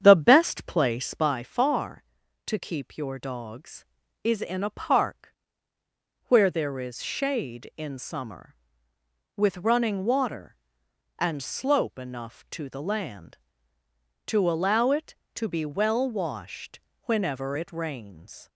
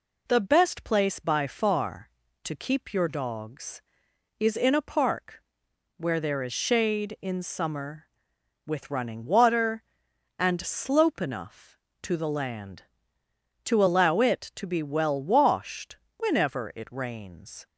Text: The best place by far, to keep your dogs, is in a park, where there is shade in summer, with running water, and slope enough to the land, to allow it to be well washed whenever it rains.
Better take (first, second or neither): second